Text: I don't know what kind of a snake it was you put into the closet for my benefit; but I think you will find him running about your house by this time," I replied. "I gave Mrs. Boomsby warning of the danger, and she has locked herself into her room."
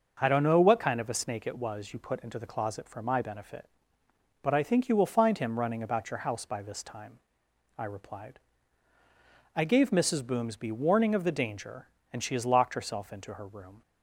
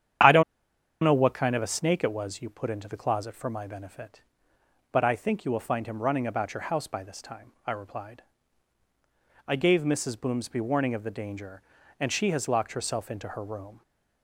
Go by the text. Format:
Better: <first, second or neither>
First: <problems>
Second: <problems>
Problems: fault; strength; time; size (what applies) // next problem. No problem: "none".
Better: first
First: starts louder than the rest; until 1.2 s; 6.5 dB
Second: starts louder than the rest; strong; until 1.8 s; 9 dB // pauses between "don't" and "know"; noticeable; at 0.4 s; 0.60 s long